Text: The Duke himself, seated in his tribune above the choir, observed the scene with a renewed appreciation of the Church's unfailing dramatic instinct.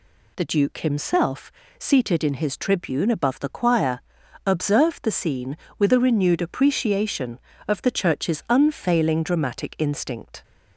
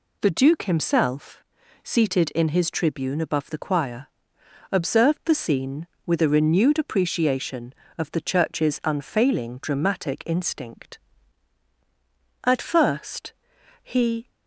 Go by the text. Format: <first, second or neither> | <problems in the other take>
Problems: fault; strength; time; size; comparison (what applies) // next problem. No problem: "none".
first | goes on to say "At first he"; strong; from 12.4 s on; 1.8 s long